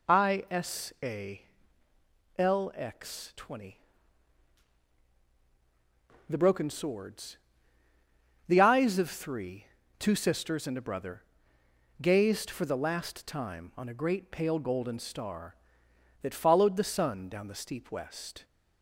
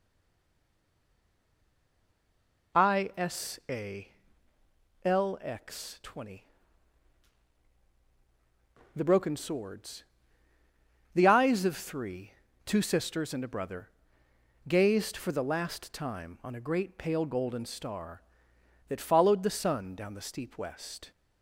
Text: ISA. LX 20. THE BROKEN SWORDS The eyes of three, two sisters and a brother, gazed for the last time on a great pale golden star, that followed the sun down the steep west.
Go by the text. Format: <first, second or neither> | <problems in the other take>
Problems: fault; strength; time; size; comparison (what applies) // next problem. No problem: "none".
first | stays silent before the first word; strong; until 2.7 s; 2.7 s long // pauses between "SWORDS" and "The"; at 10.0 s; 1.1 s long; also in the first